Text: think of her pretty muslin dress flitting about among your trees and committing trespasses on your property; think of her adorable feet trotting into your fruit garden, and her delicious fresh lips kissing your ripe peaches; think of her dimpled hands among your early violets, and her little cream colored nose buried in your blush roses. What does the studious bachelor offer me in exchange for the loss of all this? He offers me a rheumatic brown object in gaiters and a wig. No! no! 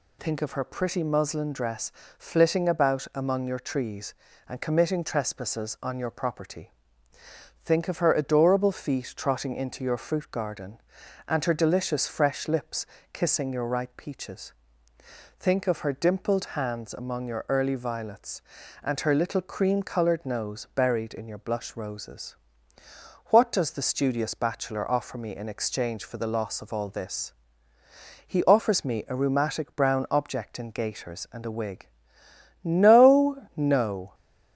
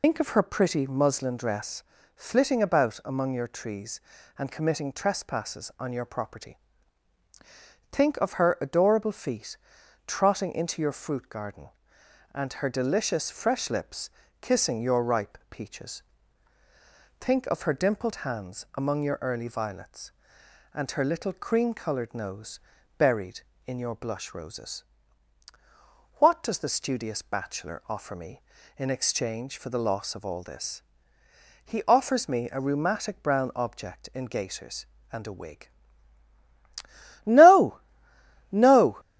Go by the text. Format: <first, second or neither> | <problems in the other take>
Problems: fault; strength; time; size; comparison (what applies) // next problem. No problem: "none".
first | loses the start of "think"; at 0.0 s; 120 ms // pauses between "dress" and "flitting"; slight; at 1.8 s; 0.34 s long; slight in the first // pauses between "feet" and "trotting"; noticeable; at 9.5 s; 0.50 s long // pauses between "lips" and "kissing"; slight; at 14.0 s; 0.32 s long; slight in the first // pauses between "nose" and "buried"; at 22.5 s; 0.38 s long